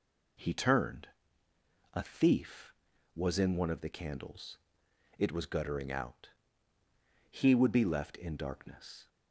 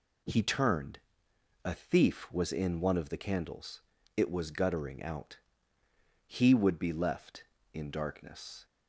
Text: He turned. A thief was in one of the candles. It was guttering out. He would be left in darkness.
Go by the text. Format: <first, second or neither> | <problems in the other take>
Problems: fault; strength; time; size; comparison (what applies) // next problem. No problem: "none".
neither | none